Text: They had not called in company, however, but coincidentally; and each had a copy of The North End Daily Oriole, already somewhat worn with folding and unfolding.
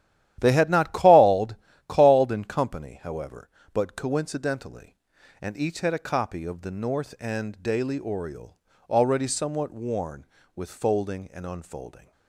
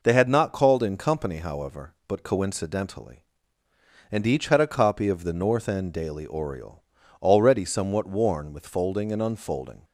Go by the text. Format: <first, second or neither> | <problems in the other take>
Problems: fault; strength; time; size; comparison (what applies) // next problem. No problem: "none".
second | starts louder than the rest; strong; until 1.4 s; 12 dB // says "called" twice; at 1.8 s